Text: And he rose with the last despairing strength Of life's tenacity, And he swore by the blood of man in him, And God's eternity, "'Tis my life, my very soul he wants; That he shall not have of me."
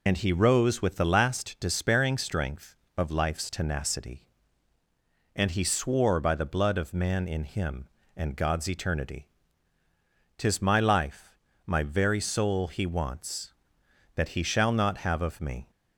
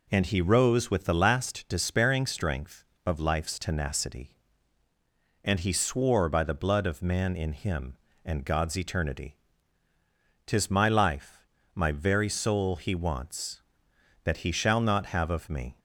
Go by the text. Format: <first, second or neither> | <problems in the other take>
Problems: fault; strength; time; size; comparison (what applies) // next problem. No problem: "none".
second | loses the start of "And"; at 0.0 s; 70 ms